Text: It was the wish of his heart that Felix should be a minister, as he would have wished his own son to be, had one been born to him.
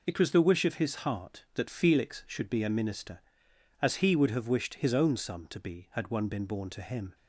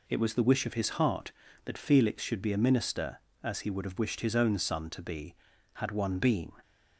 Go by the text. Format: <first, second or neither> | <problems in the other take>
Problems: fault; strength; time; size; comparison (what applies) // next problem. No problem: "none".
first | stops before "born to him"; at 6.6 s